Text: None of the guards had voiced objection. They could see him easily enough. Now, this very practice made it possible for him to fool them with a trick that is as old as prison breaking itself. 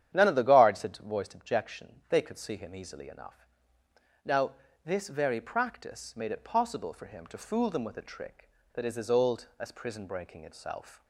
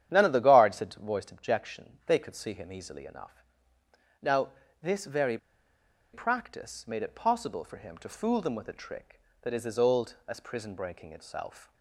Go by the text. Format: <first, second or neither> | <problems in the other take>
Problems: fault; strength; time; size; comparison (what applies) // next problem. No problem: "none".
first | starts louder than the rest; strong; until 1.1 s; 10 dB; strong in the first // pauses between "very" and "practice"; noticeable; at 5.3 s; 0.76 s long